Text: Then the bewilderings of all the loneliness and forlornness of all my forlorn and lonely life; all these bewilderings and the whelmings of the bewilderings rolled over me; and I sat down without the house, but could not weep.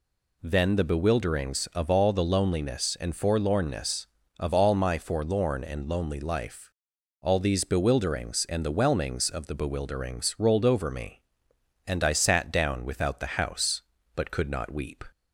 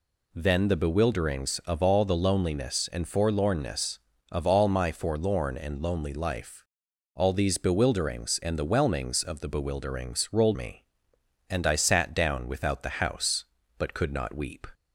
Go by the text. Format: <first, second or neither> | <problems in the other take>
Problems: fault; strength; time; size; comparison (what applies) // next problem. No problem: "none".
first | skips "over"; at 10.5 s